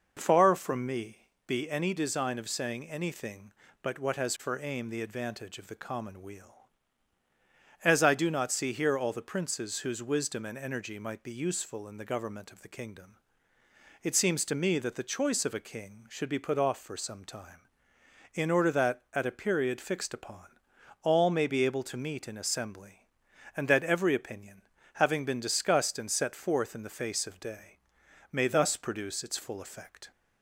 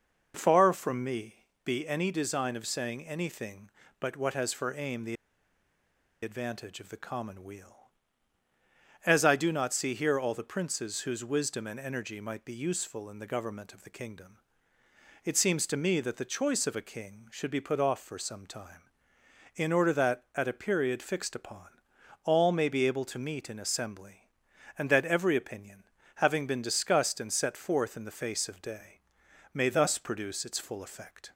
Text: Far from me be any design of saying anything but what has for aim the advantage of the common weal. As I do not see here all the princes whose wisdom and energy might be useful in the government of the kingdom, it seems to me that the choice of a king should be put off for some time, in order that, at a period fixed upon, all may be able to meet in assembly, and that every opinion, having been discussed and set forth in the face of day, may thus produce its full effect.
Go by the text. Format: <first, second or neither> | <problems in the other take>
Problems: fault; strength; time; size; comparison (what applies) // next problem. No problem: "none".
first | pauses between "me" and "be"; slight; at 1.4 s; 0.18 s long; slight in the first // pauses between "the" and "advantage"; at 5.1 s; 1.0 s long